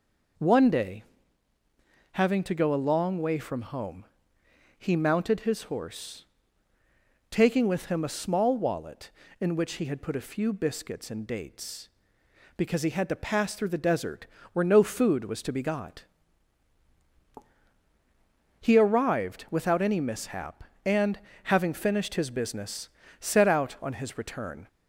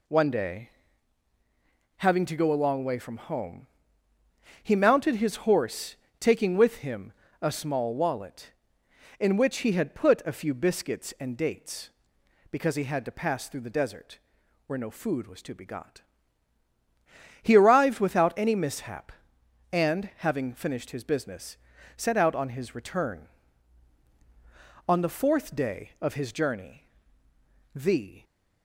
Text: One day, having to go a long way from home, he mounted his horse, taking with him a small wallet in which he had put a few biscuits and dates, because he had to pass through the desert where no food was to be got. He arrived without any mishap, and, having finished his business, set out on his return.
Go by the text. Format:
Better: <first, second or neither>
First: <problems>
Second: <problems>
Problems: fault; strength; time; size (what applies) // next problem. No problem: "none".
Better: first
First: pauses between "desert" and "where"; slight; at 14.2 s; 0.26 s long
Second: pauses between "him" and "a"; slight; at 7.1 s; 0.26 s long // pauses between "desert" and "where"; noticeable; at 14.1 s; 0.46 s long // goes on to say "On the fourth day of his journey the"; strong; from 24.8 s on; 3.3 s long